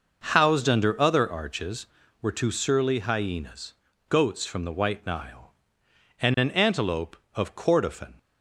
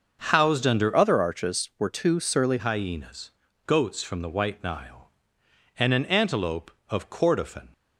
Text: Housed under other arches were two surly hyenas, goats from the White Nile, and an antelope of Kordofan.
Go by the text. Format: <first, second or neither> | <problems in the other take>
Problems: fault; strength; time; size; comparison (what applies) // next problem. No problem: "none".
first | starts louder than the rest; until 1.3 s; 6.5 dB // changes voice from "other" to "surly"; from 0.9 to 2.5 s; 1.6 s long